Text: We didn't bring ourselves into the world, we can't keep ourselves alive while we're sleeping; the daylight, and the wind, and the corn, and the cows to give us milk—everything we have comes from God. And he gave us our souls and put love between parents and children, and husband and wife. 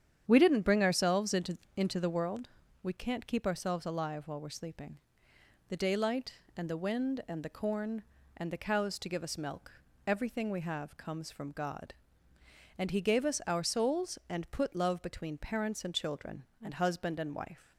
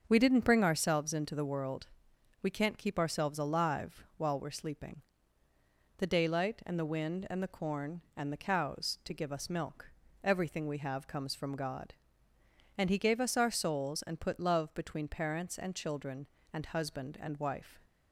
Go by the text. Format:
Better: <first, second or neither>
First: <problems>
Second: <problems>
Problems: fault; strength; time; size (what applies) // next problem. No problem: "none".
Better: second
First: starts louder than the rest; strong; until 1.2 s; 9 dB // says "into" twice; at 1.7 s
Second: starts louder than the rest; until 1.0 s; 7 dB